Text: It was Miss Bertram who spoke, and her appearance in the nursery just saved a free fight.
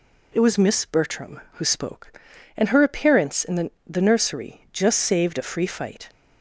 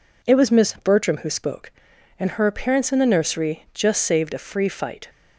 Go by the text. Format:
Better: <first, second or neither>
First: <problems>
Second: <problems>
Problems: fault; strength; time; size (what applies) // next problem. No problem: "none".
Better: second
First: says "the" twice; at 3.8 s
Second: none